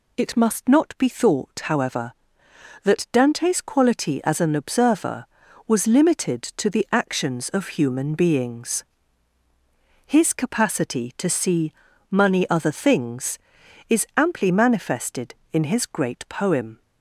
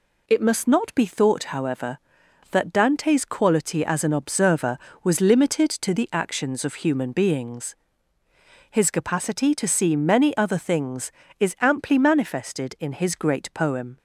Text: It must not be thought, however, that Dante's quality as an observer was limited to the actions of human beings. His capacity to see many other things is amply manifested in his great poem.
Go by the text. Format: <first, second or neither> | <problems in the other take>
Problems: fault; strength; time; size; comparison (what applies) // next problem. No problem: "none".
second | says "money" for "many"; at 12.0 s